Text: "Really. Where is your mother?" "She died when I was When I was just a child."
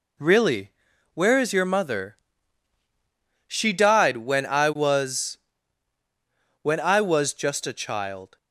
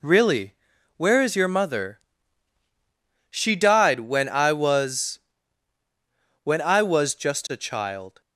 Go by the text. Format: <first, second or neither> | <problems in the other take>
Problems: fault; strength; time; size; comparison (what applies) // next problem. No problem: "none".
neither | pauses between "was" and "When"; the same in both